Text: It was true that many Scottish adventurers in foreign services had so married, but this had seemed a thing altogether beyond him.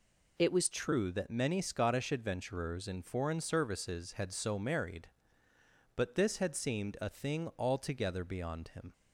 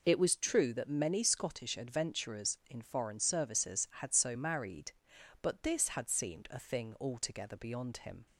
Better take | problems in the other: second | changes voice at "true"; from 0.7 s on; 8.2 s long

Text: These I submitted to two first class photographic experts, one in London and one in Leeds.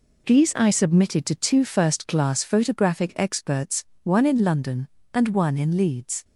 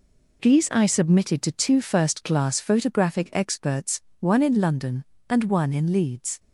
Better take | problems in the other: neither | none

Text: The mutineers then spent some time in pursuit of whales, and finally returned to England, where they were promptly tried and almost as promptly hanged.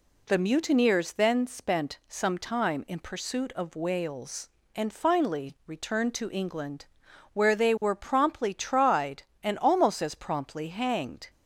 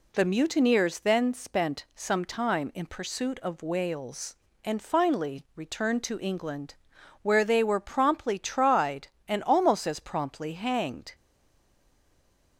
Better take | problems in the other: first | stays silent after the last word; noticeable; from 11.1 s on; 1.4 s long

